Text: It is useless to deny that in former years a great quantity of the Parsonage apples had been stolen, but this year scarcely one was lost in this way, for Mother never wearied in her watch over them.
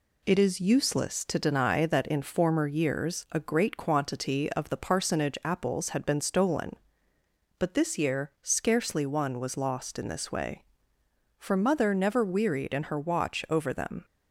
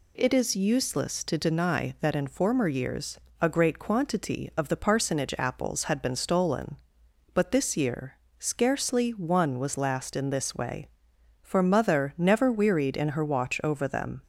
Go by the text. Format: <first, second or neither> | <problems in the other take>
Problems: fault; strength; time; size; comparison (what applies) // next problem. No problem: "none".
first | pauses between "years" and "a"; slight; at 3.1 s; 0.24 s long // pauses between "year" and "scarcely"; slight; at 8.1 s; 0.24 s long // says "last" for "lost"; at 9.7 s